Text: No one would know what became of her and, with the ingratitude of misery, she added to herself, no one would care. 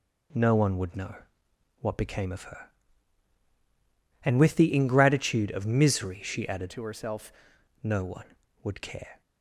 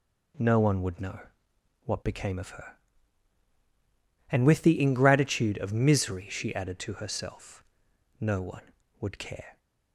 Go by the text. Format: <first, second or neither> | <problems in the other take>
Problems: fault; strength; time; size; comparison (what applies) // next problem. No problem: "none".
second | pauses between "know" and "what"; noticeable; at 1.1 s; 0.66 s long; noticeable in the second // changes voice from "to" to "herself"; from 6.7 to 7.3 s; 0.6 s long